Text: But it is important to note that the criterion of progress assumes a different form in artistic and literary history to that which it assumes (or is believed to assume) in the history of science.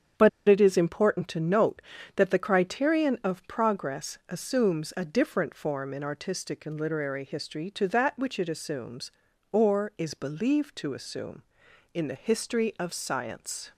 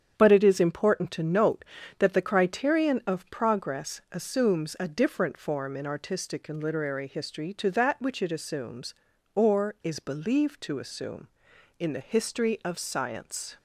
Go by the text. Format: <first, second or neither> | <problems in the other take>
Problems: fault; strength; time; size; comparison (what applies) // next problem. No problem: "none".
second | starts louder than the rest; strong; until 1.3 s; 8 dB; strong in the second // pauses between "But" and "it"; slight; at 0.2 s; 0.18 s long